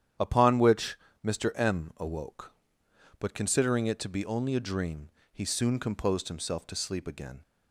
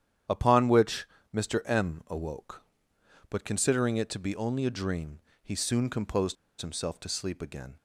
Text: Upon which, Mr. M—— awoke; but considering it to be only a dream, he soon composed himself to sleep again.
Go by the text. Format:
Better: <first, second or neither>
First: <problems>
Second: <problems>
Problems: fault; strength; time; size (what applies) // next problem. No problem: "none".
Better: first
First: starts louder than the rest; strong; until 1.4 s; 10 dB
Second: starts louder than the rest; strong; until 1.5 s; 10 dB // pauses between "composed" and "himself"; slight; at 6.3 s; 0.24 s long